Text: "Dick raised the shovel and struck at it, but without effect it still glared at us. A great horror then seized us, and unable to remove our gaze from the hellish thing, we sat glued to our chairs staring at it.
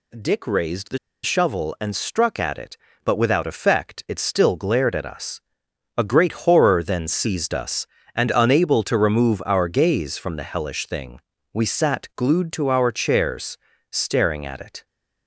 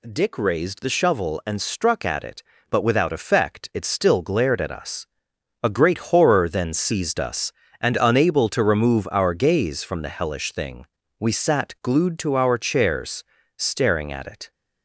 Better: second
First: pauses between "the" and "shovel"; slight; at 0.9 s; 0.25 s long // pauses between "chairs" and "staring"; slight; at 13.5 s; 0.34 s long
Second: pauses between "chairs" and "staring"; slight; at 13.2 s; 0.34 s long

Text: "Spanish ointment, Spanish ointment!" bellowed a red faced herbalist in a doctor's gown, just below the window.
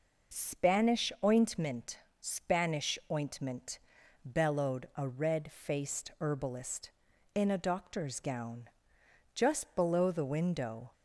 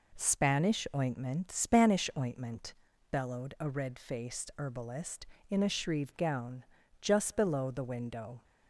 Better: first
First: none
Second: says "shrieve" for "doctor's"; at 5.6 s

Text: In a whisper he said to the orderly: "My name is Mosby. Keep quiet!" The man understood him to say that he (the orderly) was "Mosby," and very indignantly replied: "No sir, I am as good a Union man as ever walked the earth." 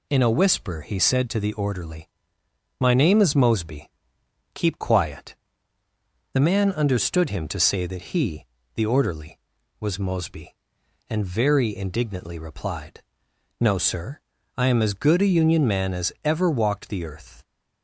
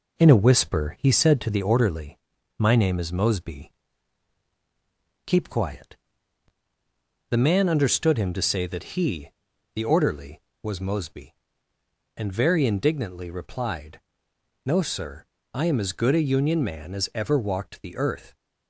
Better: first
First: none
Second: starts louder than the rest; until 1.6 s; 4 dB

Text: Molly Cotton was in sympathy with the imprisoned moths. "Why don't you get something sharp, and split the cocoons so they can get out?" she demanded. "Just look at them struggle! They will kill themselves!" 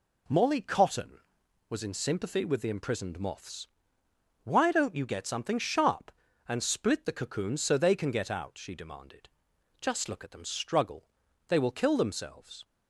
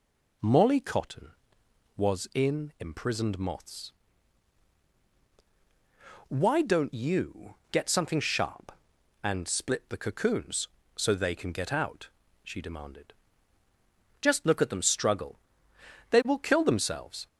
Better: first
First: none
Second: skips "sympathy with the"; at 2.7 s // pauses between "you" and "get"; slight; at 7.5 s; 0.16 s long

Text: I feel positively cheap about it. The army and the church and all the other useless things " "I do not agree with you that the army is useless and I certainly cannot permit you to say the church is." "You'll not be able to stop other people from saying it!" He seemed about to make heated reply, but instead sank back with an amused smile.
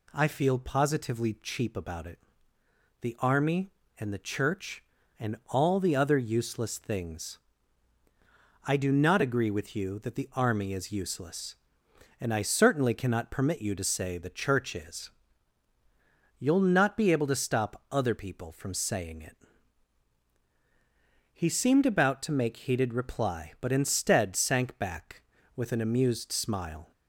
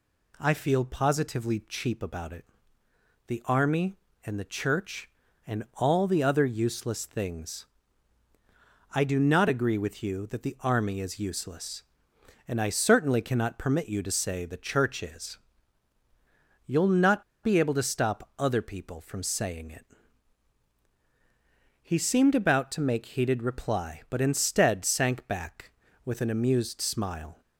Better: first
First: none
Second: pauses between "not" and "be"; slight; at 17.2 s; 0.20 s long

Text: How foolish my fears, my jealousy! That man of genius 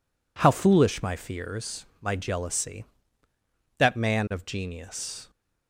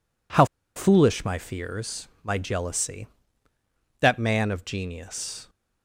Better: first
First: none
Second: pauses between "How" and "foolish"; slight; at 0.4 s; 0.30 s long

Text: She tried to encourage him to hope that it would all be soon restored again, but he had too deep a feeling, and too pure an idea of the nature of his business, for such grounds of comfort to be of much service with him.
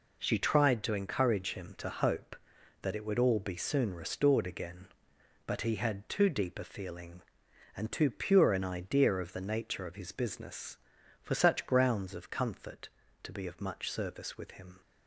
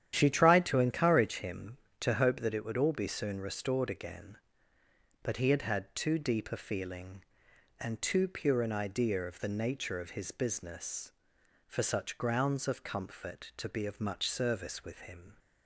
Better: first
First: none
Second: starts louder than the rest; strong; until 1.1 s; 10 dB // says "had" twice; at 5.6 s

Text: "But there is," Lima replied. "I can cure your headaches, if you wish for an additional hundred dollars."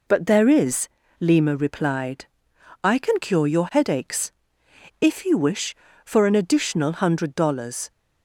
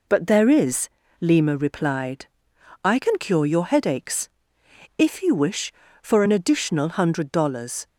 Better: neither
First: none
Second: none

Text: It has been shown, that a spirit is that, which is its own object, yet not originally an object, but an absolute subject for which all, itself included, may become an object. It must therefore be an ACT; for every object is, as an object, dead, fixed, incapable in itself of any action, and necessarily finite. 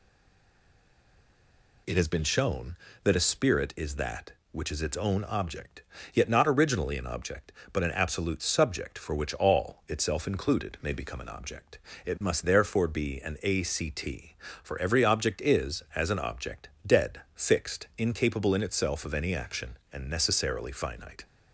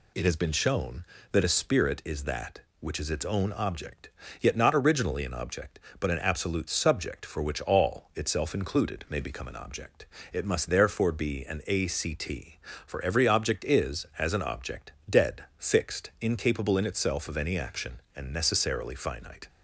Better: second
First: stays silent before the first word; noticeable; until 1.8 s; 1.8 s long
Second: none

